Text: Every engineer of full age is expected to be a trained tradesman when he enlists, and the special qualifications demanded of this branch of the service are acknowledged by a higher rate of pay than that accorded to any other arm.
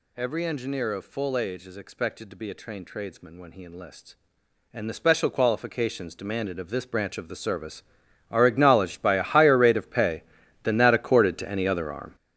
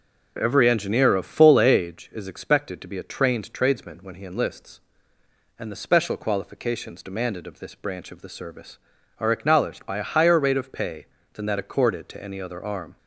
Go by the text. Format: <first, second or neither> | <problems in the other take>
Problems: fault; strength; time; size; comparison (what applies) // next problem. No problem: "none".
second | gets louder; strong; throughout; 11.5 dB